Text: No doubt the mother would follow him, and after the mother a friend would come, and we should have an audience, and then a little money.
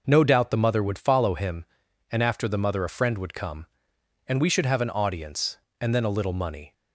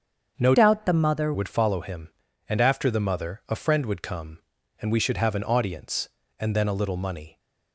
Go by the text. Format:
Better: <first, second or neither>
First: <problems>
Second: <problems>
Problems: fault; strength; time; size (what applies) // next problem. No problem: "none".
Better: first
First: none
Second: starts louder than the rest; until 1.3 s; 7 dB // changes voice from "doubt" to "mother"; from 0.5 to 1.3 s; 0.8 s long